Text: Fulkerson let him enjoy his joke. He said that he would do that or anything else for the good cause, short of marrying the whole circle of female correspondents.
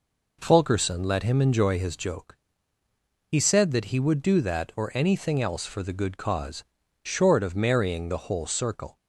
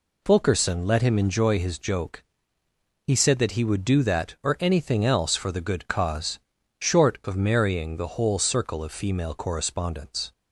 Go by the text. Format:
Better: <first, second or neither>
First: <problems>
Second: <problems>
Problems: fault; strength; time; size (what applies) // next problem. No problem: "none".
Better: second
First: stops before "of female correspondents"; at 8.9 s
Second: none